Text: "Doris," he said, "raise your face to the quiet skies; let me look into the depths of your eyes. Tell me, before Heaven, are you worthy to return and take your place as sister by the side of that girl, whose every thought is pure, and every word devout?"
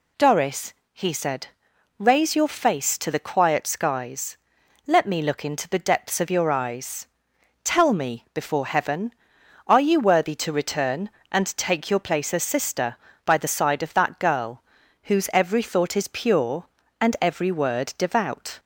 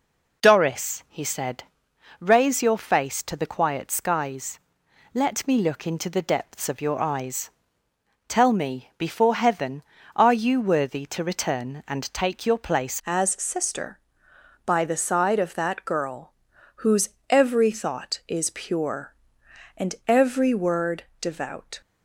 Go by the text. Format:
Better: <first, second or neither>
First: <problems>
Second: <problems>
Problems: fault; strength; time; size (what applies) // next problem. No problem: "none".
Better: first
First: none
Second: changes voice at "as"; from 13.0 s on; 8.8 s long // pauses between "whose" and "every"; slight; at 17.0 s; 0.22 s long // pauses between "word" and "devout"; slight; at 21.0 s; 0.16 s long